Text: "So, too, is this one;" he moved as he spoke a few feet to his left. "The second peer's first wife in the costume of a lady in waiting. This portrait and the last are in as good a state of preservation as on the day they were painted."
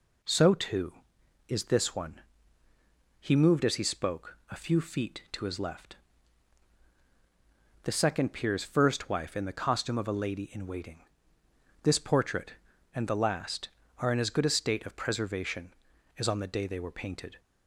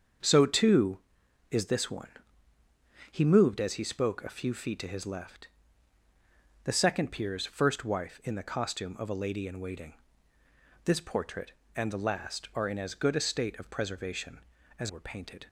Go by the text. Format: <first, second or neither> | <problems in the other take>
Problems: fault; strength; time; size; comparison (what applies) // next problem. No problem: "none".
first | starts louder than the rest; until 1.7 s; 7 dB // skips "on the day they"; at 14.8 s